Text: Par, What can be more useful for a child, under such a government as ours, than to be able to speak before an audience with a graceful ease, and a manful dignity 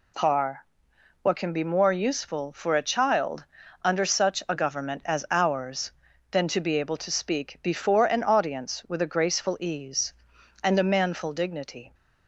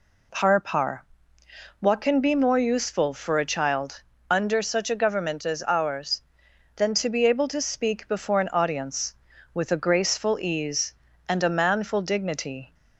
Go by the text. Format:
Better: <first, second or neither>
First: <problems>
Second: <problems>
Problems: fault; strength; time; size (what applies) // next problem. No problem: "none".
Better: first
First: none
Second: says "Par" twice; at 0.5 s